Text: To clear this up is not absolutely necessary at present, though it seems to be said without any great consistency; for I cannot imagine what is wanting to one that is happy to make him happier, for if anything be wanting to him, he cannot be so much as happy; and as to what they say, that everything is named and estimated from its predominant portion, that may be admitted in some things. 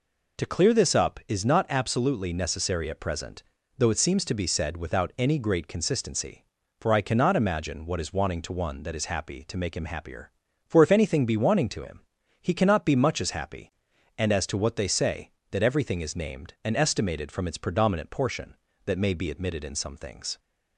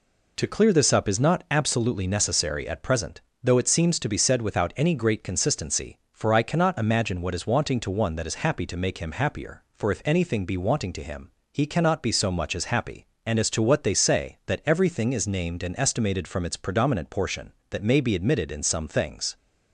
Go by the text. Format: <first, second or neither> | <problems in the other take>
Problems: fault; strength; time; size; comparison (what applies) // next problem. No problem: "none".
second | skips "so"; at 12.9 s